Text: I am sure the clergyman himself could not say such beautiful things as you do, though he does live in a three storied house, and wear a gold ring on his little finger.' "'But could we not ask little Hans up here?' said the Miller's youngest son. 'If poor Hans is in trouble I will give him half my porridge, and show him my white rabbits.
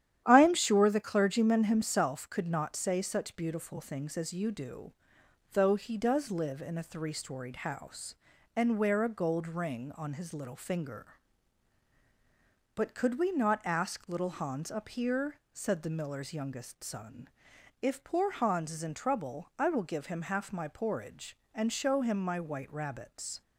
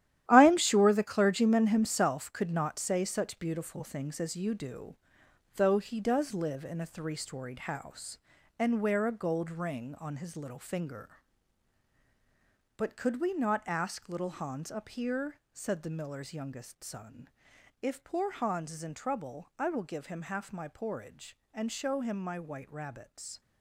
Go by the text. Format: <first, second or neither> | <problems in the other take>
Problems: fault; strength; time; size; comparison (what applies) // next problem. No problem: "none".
first | gets quieter; strong; throughout; 11.5 dB // starts louder than the rest; strong; until 1.2 s; 12.5 dB; strong in the first